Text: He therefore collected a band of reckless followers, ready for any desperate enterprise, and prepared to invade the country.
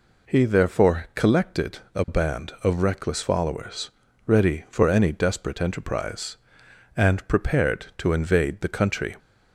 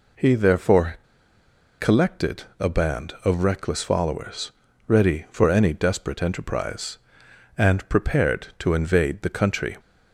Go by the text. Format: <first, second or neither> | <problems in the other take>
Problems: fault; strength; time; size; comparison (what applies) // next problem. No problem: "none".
first | pauses between "therefore" and "collected"; noticeable; at 0.9 s; 0.84 s long // pauses between "collected" and "a"; slight; at 2.4 s; 0.16 s long; slight in the first